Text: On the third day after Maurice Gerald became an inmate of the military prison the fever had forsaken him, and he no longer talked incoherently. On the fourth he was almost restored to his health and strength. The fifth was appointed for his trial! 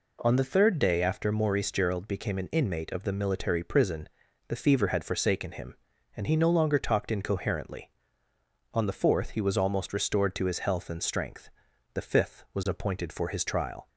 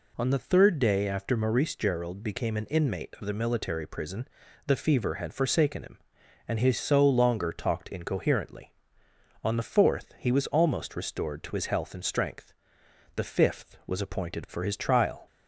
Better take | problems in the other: first | pauses between "prison" and "the"; at 4.2 s; 0.38 s long; also in the first // says "so" for "no"; at 6.7 s

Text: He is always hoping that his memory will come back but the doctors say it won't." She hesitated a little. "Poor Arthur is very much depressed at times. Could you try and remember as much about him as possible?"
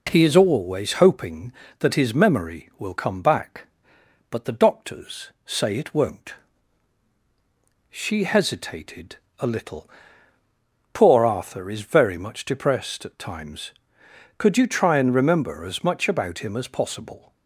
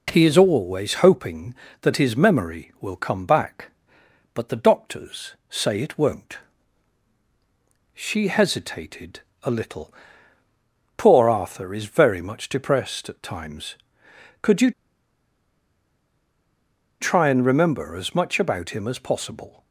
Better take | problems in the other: first | pauses between "hesitated" and "a"; slight; at 9.1 s; 0.24 s long; slight in the first // pauses between "you" and "try"; strong; at 14.7 s; 2.2 s long

